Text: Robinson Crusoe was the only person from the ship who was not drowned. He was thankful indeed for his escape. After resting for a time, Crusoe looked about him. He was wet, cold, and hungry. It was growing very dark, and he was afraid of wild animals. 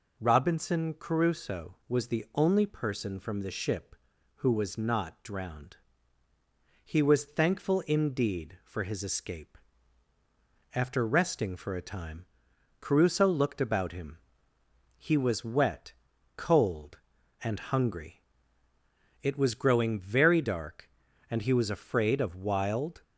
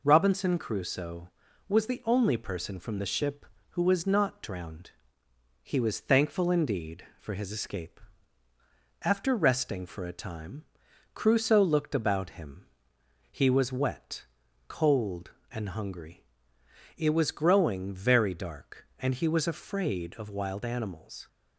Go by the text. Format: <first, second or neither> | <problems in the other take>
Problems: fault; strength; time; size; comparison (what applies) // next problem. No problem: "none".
second | stops before "animals"; at 23.0 s